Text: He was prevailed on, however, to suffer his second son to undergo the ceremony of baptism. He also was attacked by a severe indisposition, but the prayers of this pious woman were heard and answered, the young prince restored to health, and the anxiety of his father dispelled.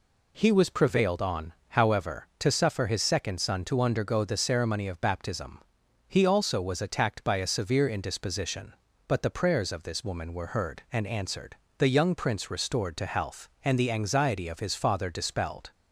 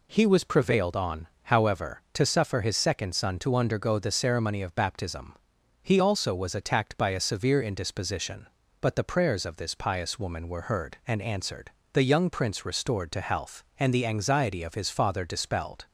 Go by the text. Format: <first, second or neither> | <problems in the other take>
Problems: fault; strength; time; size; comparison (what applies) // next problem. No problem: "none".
second | skips "pious"; at 10.0 s